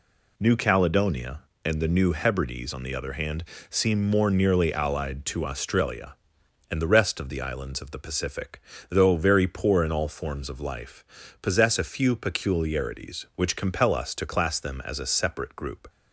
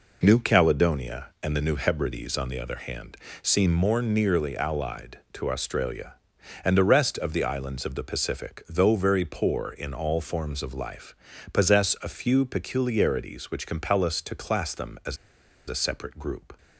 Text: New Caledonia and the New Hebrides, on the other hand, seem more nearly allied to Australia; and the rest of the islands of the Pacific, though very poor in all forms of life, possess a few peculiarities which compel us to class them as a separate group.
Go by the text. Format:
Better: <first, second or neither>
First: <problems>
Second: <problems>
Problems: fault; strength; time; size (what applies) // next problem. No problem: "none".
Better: first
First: none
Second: pauses between "as" and "a"; noticeable; at 15.1 s; 0.52 s long